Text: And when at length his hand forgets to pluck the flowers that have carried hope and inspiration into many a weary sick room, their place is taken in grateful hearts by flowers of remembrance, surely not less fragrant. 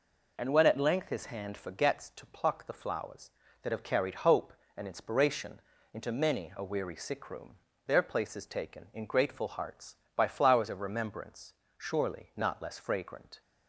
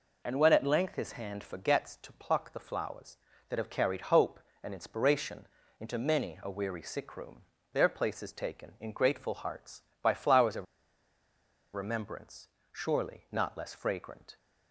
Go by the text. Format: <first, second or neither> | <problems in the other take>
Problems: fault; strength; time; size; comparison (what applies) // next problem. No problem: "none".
first | pauses between "inspiration" and "into"; slight; at 5.4 s; 0.32 s long; slight in the first // pauses between "of" and "remembrance"; at 10.6 s; 1.0 s long